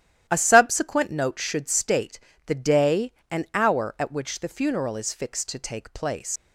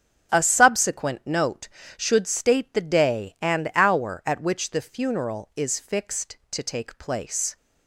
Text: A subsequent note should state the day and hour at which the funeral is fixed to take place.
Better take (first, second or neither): second